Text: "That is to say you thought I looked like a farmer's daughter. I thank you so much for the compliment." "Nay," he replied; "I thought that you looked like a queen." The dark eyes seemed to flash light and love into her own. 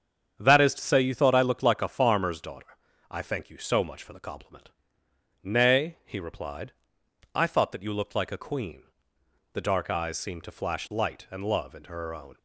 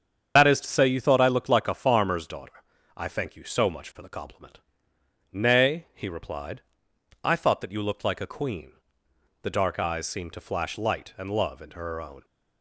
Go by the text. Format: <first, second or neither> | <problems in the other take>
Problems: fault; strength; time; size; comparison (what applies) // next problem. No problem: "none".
first | loses the start of "That"; at 0.3 s; 105 ms // starts louder than the rest; strong; until 1.3 s; 7.5 dB; strong in the first